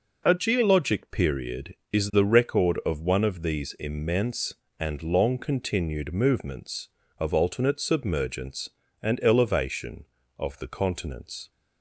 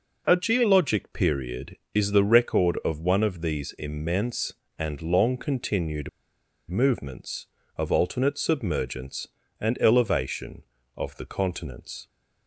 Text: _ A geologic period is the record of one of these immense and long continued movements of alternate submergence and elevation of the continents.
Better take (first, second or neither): first